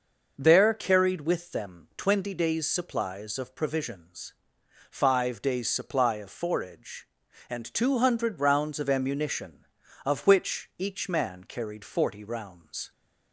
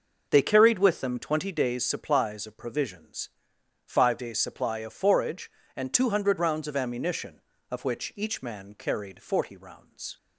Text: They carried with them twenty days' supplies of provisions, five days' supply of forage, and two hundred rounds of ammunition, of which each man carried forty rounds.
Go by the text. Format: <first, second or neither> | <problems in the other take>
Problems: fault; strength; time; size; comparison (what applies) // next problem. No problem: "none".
second | says "There" for "They"; at 0.3 s